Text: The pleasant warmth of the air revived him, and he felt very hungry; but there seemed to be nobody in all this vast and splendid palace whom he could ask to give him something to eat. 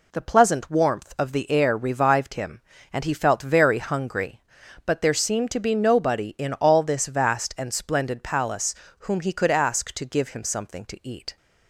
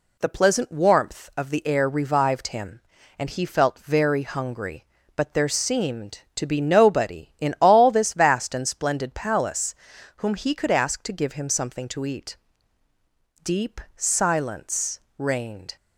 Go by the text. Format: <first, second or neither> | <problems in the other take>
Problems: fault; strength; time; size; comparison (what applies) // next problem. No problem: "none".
first | pauses between "palace" and "whom"; at 9.7 s; 0.40 s long; slight in the first // goes on to say "Deep silence reigned"; strong; from 13.4 s on; 2.3 s long